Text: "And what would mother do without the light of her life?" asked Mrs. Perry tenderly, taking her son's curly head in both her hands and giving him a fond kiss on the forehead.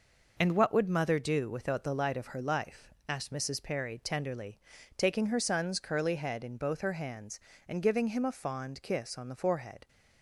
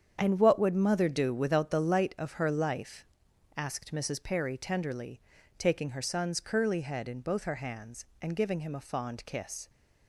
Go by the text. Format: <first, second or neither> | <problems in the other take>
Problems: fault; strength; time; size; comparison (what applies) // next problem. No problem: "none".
first | starts louder than the rest; strong; until 1.2 s; 8 dB // stops before "on the forehead"; at 9.6 s